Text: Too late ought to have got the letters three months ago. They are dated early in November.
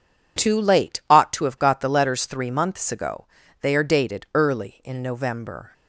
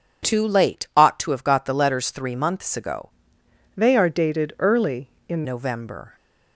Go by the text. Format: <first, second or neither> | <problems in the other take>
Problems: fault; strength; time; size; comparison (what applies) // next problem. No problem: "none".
first | changes voice from "They" to "in"; from 3.7 to 5.4 s; 1.7 s long